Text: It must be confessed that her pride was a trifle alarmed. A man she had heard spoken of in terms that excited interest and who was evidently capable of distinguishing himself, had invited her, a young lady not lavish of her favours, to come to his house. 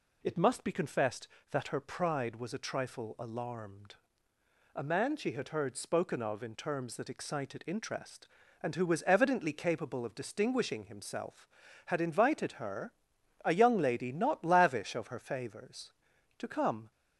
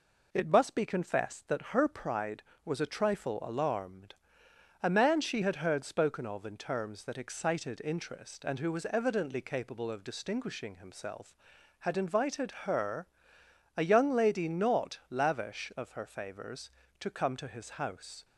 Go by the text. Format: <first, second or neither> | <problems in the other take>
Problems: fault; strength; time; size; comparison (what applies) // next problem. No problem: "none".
second | stops before "to his house"; at 16.9 s